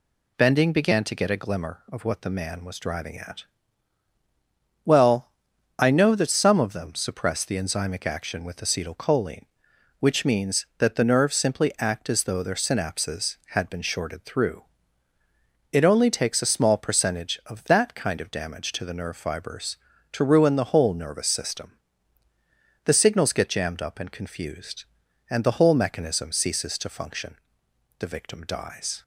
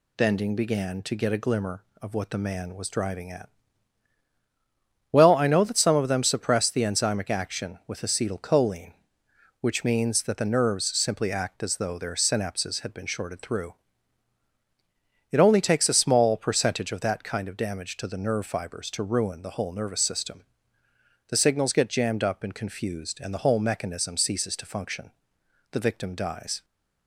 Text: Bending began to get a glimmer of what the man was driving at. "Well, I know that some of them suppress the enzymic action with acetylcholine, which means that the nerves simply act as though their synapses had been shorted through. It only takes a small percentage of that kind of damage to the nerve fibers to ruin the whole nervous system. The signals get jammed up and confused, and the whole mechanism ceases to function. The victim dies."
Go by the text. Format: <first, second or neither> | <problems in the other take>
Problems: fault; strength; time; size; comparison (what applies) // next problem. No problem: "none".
neither | none